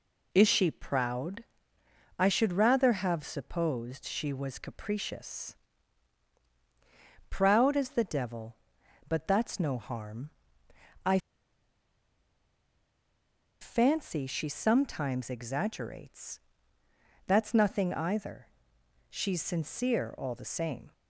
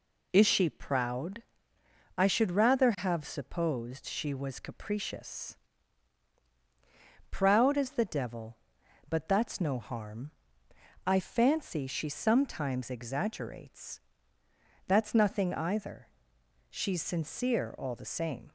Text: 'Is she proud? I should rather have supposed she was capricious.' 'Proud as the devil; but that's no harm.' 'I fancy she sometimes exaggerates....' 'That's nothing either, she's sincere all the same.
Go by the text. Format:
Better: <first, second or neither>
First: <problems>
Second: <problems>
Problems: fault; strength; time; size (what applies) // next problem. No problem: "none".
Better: second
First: pauses between "I" and "fancy"; strong; at 11.1 s; 2.4 s long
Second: none